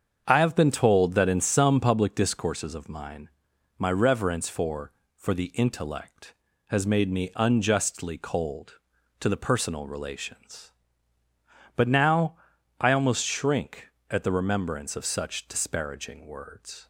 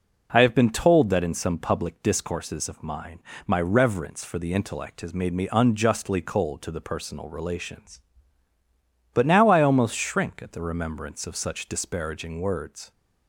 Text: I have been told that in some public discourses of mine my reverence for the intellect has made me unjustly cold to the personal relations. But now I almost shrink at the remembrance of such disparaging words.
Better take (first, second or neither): second